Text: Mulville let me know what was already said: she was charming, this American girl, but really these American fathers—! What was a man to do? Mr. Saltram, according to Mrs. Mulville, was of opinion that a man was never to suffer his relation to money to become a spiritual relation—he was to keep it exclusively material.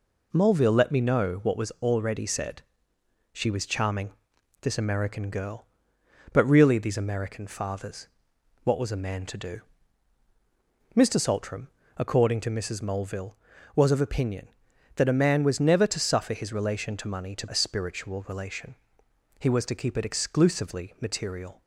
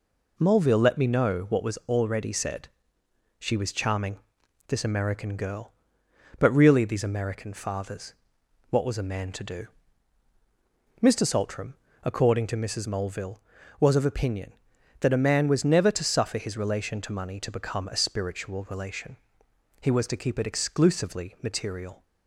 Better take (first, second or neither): second